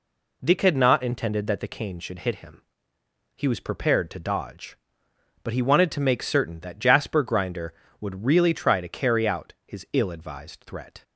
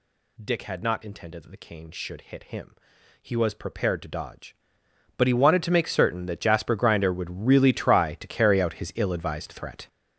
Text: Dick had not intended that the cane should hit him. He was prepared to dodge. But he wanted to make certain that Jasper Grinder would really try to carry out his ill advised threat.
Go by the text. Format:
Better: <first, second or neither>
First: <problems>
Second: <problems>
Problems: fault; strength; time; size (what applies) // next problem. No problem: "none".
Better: first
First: none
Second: gets louder; strong; throughout; 11 dB